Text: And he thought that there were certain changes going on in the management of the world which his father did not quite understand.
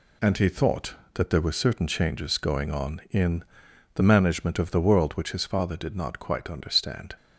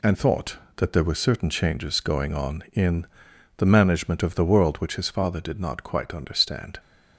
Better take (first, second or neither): first